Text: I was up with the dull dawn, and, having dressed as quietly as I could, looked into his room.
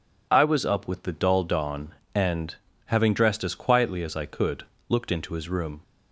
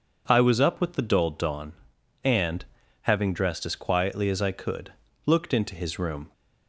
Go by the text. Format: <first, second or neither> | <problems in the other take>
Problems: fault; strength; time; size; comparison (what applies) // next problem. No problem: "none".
neither | none